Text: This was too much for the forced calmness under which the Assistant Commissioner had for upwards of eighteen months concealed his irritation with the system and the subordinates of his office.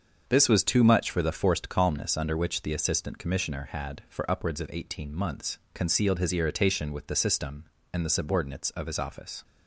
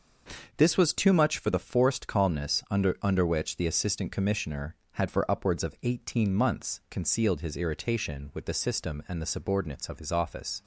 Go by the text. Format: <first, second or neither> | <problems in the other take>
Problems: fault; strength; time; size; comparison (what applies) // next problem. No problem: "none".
first | starts louder than the rest; until 1.5 s; 6.5 dB; also in the first // says "under" twice; at 3.0 s